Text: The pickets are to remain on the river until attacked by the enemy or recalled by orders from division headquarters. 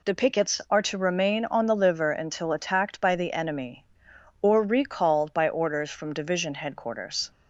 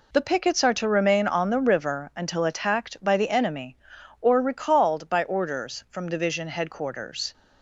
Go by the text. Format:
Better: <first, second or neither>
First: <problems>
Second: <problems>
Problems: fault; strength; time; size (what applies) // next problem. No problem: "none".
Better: second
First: says "liver" for "river"; at 1.7 s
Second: none